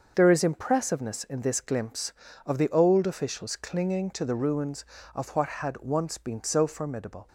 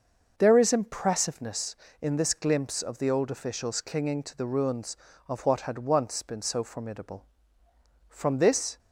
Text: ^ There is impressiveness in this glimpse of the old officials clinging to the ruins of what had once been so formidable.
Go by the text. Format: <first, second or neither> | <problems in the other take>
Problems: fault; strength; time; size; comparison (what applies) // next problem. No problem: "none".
first | starts louder than the rest; noticeable; until 1.3 s; 6 dB; also in the first // goes on to say "From this"; noticeable; from 8.0 s on; 0.70 s long